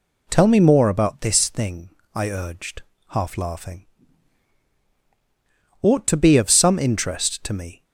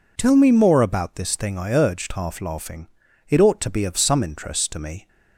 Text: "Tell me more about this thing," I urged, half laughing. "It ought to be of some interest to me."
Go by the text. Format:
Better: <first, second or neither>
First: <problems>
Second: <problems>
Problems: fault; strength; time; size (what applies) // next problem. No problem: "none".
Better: second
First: skips "It"; at 4.8 s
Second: none